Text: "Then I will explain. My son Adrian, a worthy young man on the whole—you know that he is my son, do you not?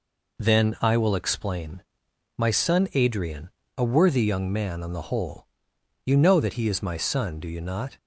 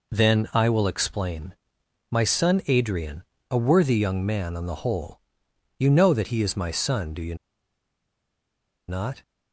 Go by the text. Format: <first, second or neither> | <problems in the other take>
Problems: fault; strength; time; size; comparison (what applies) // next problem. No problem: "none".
first | pauses between "you" and "not"; strong; at 7.3 s; 1.5 s long